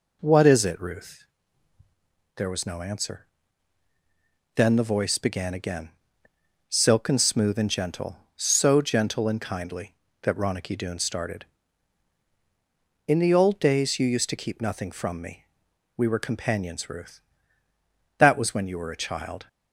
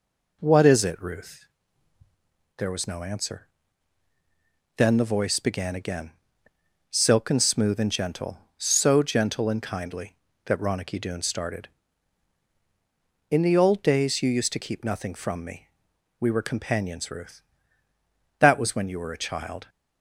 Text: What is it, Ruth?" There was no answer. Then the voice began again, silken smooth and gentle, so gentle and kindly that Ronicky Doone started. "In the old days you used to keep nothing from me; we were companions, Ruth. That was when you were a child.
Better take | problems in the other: neither | none

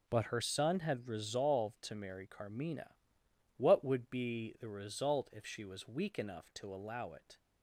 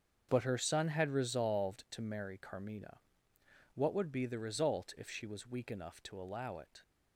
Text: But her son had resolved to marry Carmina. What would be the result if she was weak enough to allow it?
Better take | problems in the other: neither | starts louder than the rest; the same in both

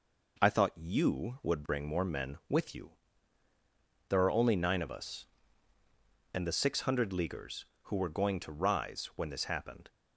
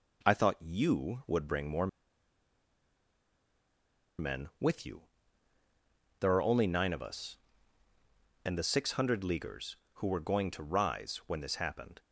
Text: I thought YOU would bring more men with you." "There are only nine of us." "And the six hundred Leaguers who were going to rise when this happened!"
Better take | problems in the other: first | pauses between "more" and "men"; strong; at 1.8 s; 2.3 s long

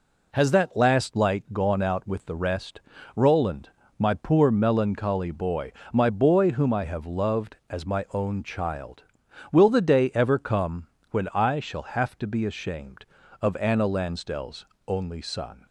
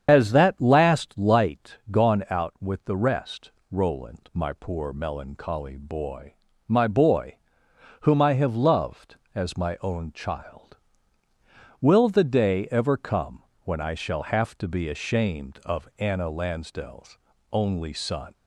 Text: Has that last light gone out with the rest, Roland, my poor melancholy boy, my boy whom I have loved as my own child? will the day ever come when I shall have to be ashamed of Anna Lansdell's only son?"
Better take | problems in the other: first | loses the start of "Has"; at 0.0 s; 55 ms // starts louder than the rest; strong; until 1.0 s; 8 dB // pauses between "boy" and "whom"; noticeable; at 7.3 s; 0.66 s long // pauses between "come" and "when"; slight; at 13.4 s; 0.20 s long; slight in the first // pauses between "Lansdell's" and "only"; slight; at 17.1 s; 0.36 s long; slight in the first

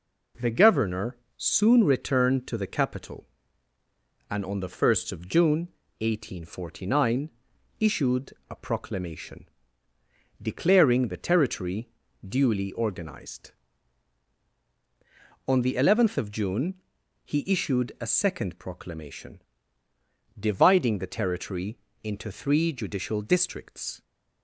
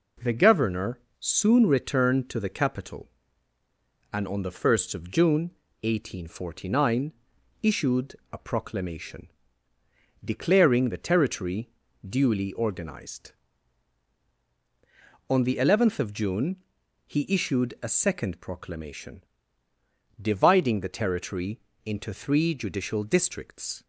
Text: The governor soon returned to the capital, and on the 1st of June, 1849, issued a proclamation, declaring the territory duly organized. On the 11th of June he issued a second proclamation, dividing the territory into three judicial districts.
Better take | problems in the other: neither | pauses between "governor" and "soon"; slight; the same in both // pauses between "issued" and "a"; slight; the same in both // pauses between "territory" and "duly"; the same in both // pauses between "June" and "he"; noticeable; the same in both // pauses between "territory" and "into"; slight; the same in both

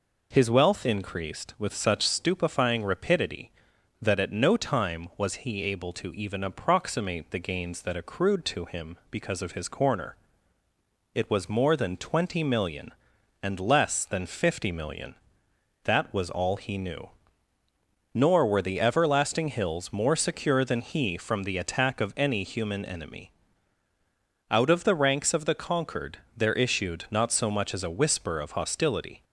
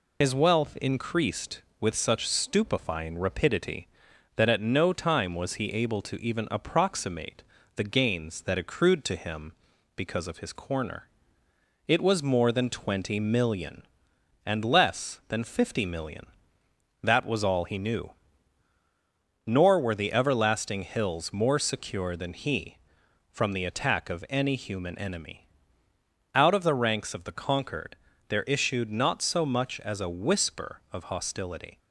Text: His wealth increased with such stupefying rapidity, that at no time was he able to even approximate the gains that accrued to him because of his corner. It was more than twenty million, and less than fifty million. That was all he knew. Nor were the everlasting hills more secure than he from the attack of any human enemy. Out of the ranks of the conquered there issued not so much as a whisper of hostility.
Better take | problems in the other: first | loses the start of "His"; at 0.2 s; 65 ms // pauses between "approximate" and "the"; slight; at 7.4 s; 0.32 s long // pauses between "conquered" and "there"; slight; at 27.9 s; 0.32 s long; slight in the first

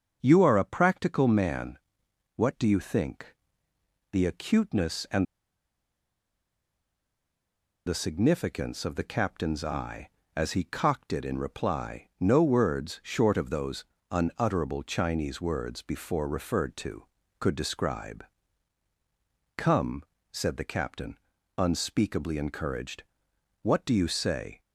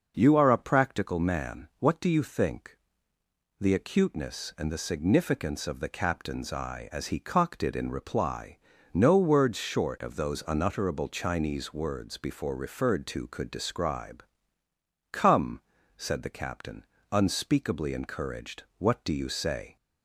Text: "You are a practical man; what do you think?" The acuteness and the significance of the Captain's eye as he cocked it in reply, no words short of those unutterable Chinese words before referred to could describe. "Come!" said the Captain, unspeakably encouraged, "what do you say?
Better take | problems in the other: second | starts louder than the rest; until 1.2 s; 6.5 dB // pauses between "and" and "the"; strong; at 5.2 s; 2.6 s long // pauses between "those" and "unutterable"; slight; at 13.8 s; 0.26 s long

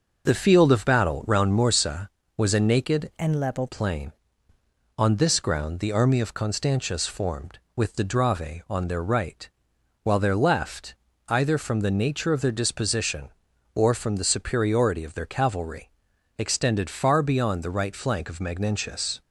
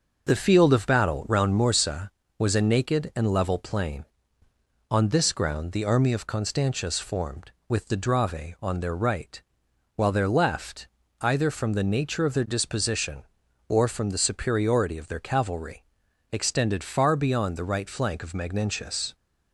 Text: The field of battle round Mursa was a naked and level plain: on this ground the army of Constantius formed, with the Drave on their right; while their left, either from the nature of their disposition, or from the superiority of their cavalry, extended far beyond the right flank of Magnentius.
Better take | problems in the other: second | changes voice from "and" to "level"; from 3.1 to 3.6 s; 0.5 s long

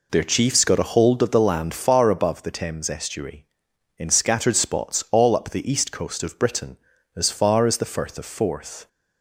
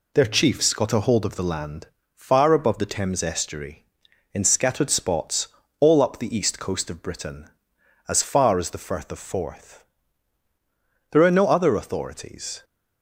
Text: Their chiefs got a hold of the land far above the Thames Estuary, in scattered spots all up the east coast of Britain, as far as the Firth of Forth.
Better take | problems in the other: first | pauses between "land" and "far"; slight; at 1.8 s; 0.28 s long // pauses between "spots" and "all"; slight; at 5.4 s; 0.30 s long // goes on to say "There are no other authorities"; from 11.0 s on; 1.5 s long

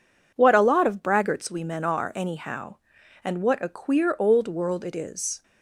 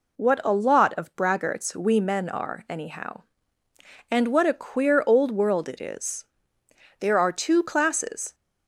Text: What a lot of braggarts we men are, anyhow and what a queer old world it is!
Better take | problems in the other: first | goes on to say "There are two classes"; from 6.9 s on; 1.3 s long

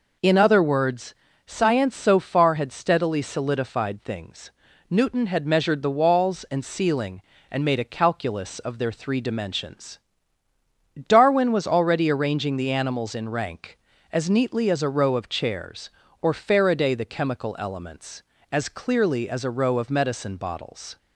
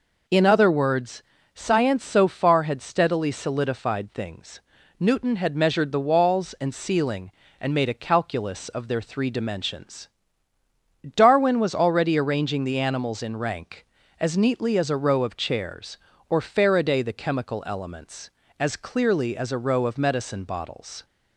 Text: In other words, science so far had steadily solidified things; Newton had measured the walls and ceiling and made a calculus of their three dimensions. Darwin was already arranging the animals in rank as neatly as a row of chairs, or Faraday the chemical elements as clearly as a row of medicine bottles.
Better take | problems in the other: neither | none

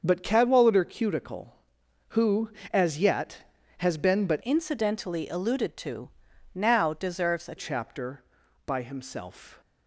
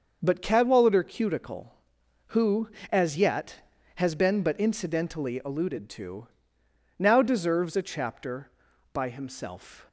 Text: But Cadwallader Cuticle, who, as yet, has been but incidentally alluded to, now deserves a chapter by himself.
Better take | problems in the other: second | starts louder than the rest; until 1.0 s; 6.5 dB; also in the second // changes voice from "incidentally" to "a"; from 4.4 to 7.5 s; 3.1 s long

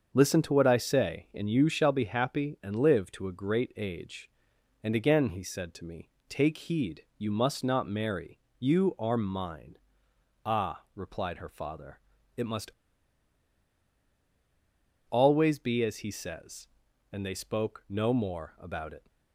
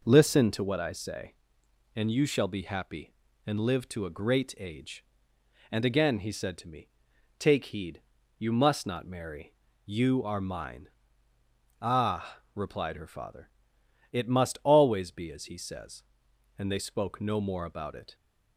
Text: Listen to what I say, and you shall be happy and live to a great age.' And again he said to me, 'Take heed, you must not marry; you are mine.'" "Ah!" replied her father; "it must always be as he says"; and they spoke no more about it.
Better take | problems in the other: second | starts louder than the rest; until 1.1 s; 6.5 dB // pauses between "must" and "always"; strong; at 12.7 s; 2.3 s long

